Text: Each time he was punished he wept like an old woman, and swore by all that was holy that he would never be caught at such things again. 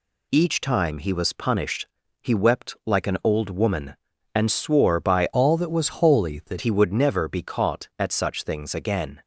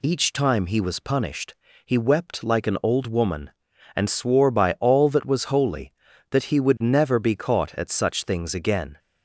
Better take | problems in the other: second | pauses between "punished" and "he"; slight; at 1.8 s; 0.34 s long; slight in the second // changes voice from "all" to "that"; from 5.3 to 6.5 s; 1.2 s long

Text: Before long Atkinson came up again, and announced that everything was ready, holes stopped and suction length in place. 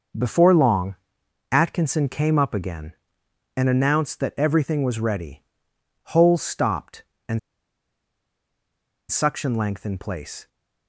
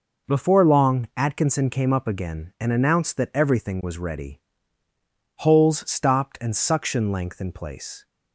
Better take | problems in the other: second | pauses between "long" and "Atkinson"; noticeable; at 0.9 s; 0.56 s long // pauses between "and" and "suction"; strong; at 7.3 s; 1.7 s long

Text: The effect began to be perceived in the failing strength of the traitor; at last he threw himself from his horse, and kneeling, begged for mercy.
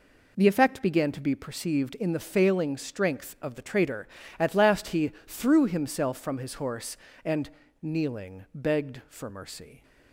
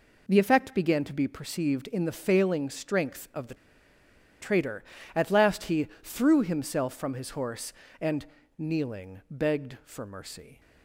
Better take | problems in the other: first | pauses between "the" and "traitor"; noticeable; at 3.5 s; 0.86 s long // pauses between "he" and "threw"; slight; at 5.8 s; 0.16 s long; slight in the first // pauses between "and" and "kneeling"; slight; at 8.2 s; 0.34 s long; slight in the first

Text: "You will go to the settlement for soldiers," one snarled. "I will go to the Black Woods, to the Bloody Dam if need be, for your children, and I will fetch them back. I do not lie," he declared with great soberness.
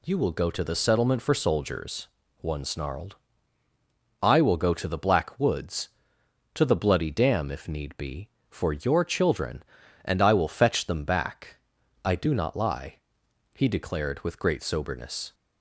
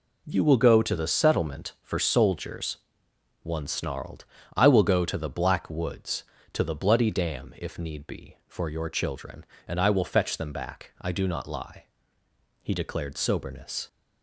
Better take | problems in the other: first | skips "with great"; at 13.1 s

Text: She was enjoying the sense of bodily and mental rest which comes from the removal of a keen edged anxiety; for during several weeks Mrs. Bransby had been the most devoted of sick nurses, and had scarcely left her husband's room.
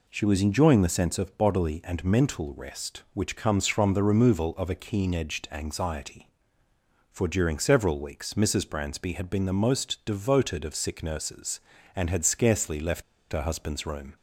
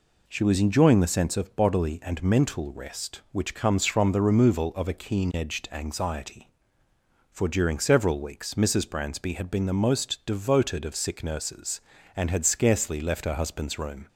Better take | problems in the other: second | pauses between "left" and "her"; slight; at 13.0 s; 0.28 s long

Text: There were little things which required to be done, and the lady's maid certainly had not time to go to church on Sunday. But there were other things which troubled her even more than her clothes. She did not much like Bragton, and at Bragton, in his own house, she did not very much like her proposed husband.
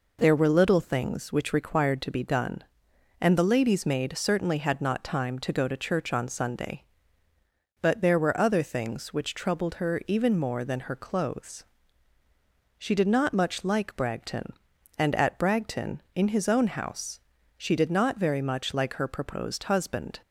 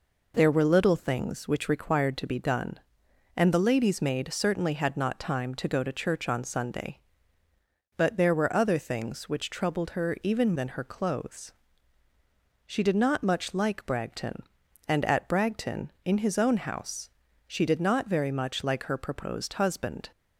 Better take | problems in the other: first | skips "more"; at 10.5 s

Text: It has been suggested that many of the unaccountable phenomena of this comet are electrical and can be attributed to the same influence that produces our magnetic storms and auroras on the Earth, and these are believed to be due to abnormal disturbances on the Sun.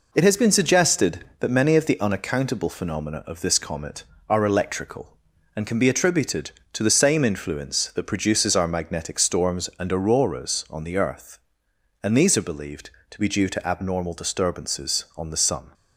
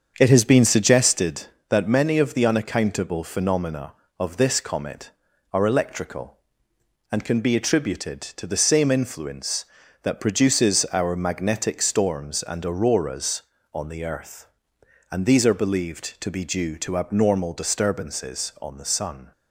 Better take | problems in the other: first | starts louder than the rest; strong; until 1.3 s; 7 dB

